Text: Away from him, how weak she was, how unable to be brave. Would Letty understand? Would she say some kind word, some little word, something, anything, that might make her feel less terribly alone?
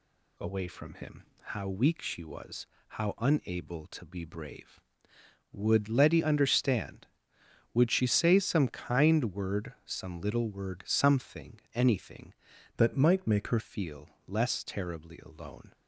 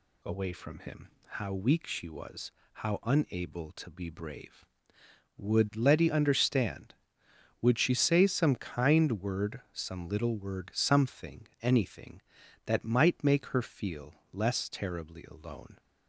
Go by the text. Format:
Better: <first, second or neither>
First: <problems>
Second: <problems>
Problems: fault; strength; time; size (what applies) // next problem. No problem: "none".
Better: second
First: changes voice from "that" to "her"; from 12.7 to 13.5 s; 0.8 s long // pauses between "feel" and "less"; slight; at 14.0 s; 0.18 s long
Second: pauses between "feel" and "less"; slight; at 14.1 s; 0.18 s long